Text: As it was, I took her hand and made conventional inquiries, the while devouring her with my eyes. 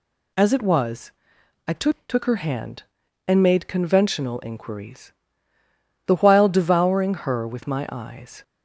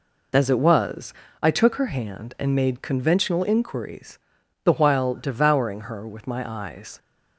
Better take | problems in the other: second | says "took" twice; at 2.0 s // pauses between "devouring" and "her"; slight; at 7.1 s; 0.16 s long

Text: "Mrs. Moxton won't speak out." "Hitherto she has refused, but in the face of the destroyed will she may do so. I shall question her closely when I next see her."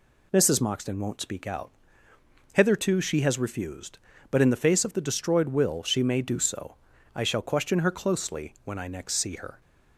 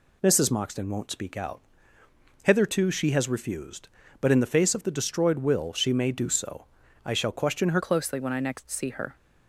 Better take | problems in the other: first | changes voice at "closely"; from 7.8 s on; 1.3 s long

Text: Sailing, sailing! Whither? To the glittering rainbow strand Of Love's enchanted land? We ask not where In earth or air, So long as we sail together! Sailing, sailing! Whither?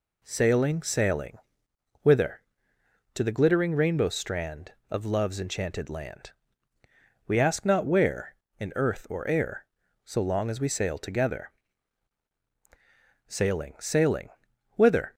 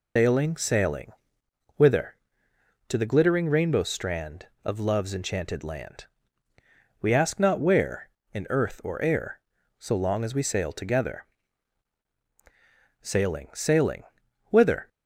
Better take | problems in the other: first | loses the start of "Sailing"; at 0.1 s; 175 ms

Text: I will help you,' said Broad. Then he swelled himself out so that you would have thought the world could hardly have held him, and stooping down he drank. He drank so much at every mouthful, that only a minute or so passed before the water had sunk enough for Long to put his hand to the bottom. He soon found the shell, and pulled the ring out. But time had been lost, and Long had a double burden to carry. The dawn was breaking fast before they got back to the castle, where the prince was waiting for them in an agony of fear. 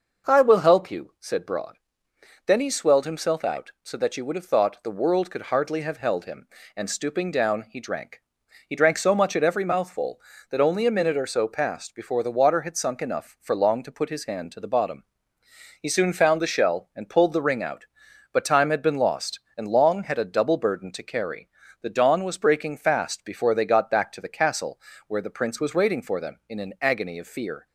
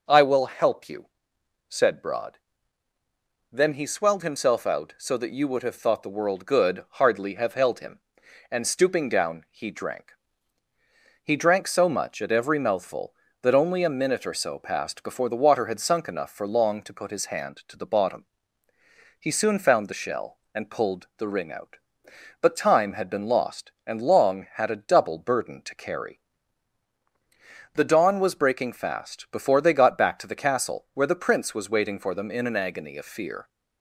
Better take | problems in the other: first | says "good" for "could"; at 6.4 s

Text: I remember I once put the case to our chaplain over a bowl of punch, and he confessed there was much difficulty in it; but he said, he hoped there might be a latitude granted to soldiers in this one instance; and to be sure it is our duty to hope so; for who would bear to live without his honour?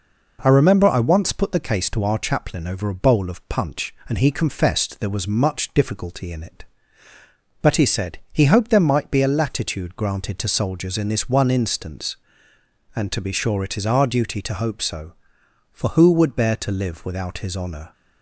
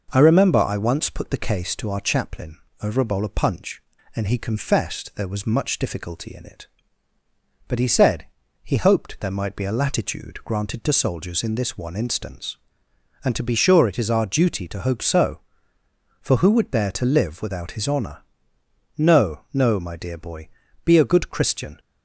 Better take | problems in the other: first | pauses between "chaplain" and "over"; slight; at 2.5 s; 0.24 s long // goes on to say "No no my dear boy be a good Christian"; strong; from 18.9 s on; 2.8 s long

